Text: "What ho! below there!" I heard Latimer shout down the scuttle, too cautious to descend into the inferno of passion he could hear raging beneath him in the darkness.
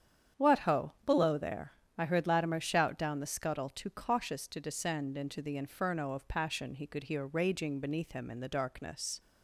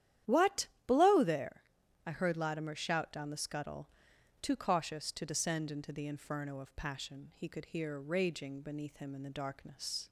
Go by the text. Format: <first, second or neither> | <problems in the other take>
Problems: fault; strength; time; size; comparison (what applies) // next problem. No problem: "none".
first | starts louder than the rest; strong; until 1.5 s; 11 dB; strong in the first // skips "ho"; at 0.7 s